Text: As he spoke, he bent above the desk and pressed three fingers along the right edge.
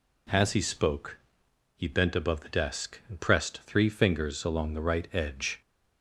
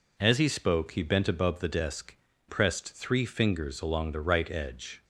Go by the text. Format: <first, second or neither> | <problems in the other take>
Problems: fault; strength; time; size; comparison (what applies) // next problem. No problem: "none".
first | skips "and"; at 2.3 s